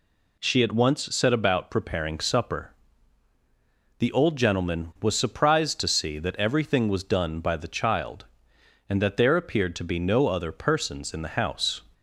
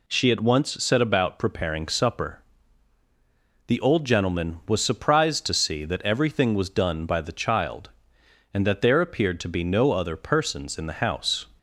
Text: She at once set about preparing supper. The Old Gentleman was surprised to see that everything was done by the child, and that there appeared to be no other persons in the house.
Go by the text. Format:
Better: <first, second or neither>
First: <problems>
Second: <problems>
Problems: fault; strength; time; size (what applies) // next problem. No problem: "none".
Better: neither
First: none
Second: none